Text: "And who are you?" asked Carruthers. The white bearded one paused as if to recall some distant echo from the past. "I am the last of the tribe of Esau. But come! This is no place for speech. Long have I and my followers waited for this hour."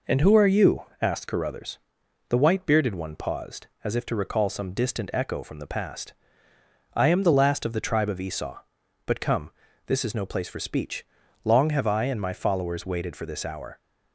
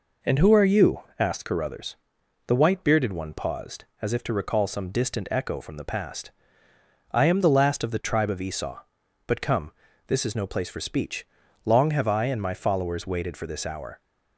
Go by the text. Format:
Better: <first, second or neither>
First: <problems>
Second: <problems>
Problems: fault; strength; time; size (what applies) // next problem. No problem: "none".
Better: neither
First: none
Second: none